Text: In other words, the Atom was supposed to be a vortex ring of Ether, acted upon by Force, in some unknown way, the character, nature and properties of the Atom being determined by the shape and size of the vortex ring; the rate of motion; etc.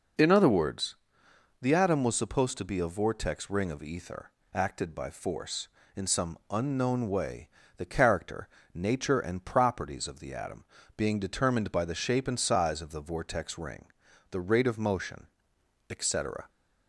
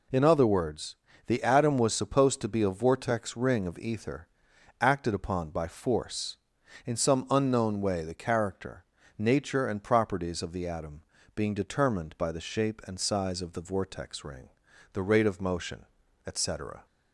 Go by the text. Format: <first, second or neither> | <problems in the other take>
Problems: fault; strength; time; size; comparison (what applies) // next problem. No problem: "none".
second | skips "upon"; at 4.9 s // pauses between "Atom" and "being"; slight; at 10.6 s; 0.32 s long; slight in the second